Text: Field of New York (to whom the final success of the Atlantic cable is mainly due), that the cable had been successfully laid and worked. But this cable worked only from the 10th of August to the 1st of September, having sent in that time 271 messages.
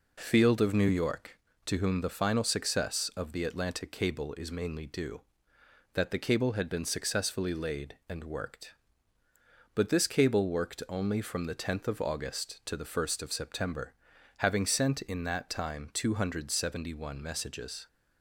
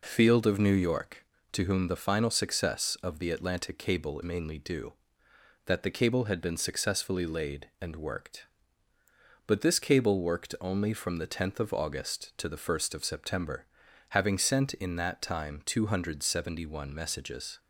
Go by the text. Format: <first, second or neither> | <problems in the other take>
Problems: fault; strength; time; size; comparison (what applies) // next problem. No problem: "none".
first | skips "is"; at 4.2 s